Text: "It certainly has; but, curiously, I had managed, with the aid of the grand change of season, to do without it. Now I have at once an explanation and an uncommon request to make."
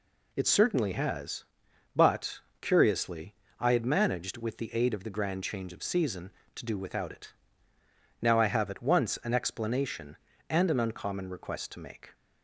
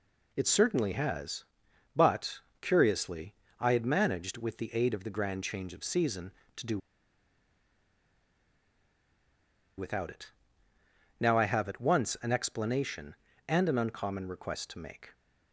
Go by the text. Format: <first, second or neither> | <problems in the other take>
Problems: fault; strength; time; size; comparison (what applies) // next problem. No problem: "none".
first | pauses between "do" and "without"; strong; at 6.7 s; 2.9 s long